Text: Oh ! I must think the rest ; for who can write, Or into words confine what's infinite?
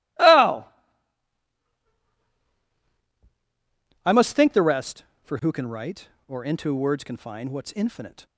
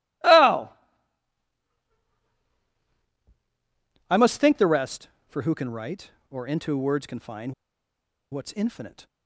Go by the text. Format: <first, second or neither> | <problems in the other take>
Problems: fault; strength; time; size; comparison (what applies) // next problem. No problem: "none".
first | pauses between "confine" and "what's"; noticeable; at 7.5 s; 0.79 s long